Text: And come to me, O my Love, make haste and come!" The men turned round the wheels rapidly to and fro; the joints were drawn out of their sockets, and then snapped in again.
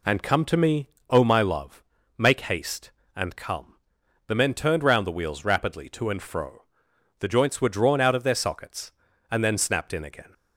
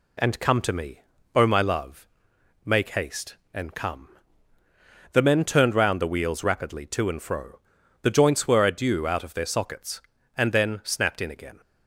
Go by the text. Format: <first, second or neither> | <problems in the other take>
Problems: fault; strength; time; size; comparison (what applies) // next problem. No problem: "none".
first | says "adieu" for "drawn"; at 8.6 s